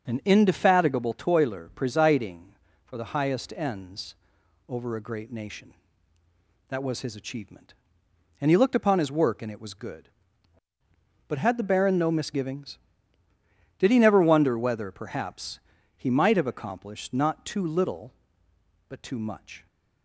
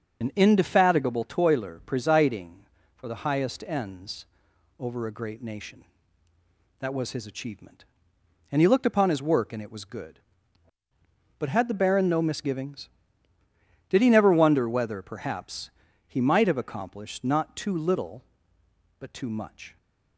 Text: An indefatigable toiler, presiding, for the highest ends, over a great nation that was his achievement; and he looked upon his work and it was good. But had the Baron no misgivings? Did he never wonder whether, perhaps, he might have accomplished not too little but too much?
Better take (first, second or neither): first